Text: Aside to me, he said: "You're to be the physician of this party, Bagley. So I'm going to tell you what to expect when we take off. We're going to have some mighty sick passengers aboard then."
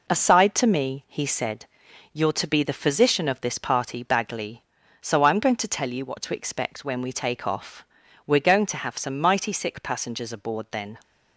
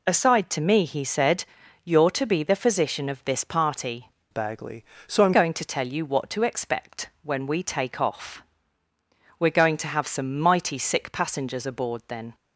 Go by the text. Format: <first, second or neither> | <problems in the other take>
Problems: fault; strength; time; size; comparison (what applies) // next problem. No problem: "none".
first | changes voice from "Bagley" to "I'm"; from 4.3 to 5.3 s; 1.0 s long